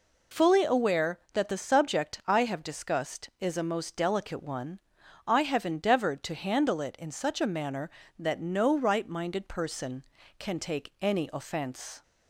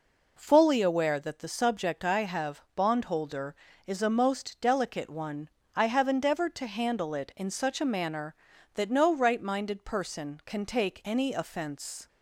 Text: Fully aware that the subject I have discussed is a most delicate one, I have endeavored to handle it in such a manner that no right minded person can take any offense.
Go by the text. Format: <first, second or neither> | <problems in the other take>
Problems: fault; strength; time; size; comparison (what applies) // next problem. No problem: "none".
first | says "bondholder" for "discussed"; at 2.7 s